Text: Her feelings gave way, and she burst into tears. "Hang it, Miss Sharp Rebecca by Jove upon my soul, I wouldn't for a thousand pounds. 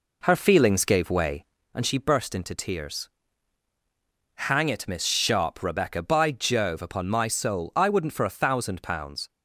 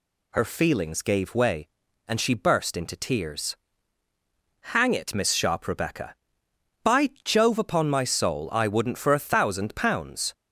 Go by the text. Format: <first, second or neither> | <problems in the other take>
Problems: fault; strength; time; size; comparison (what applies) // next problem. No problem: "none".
second | starts louder than the rest; until 1.7 s; 3.5 dB